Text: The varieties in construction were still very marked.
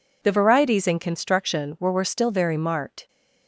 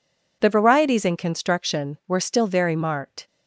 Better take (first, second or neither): second